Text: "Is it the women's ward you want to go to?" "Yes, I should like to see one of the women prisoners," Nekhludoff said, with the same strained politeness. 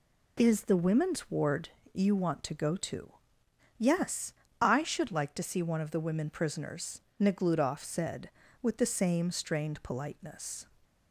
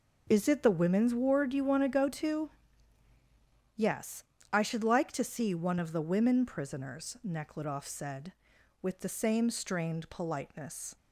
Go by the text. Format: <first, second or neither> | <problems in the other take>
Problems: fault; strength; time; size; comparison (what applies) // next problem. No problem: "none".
second | skips "it"; at 0.6 s // pauses between "ward" and "you"; slight; at 1.7 s; 0.22 s long